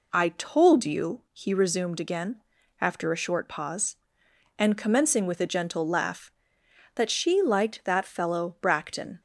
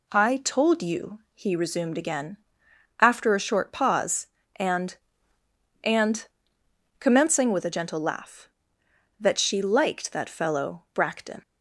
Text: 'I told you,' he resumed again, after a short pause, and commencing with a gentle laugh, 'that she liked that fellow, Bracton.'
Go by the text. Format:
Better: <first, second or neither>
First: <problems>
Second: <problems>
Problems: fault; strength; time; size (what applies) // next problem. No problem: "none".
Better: first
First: none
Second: says "and" twice; at 5.8 s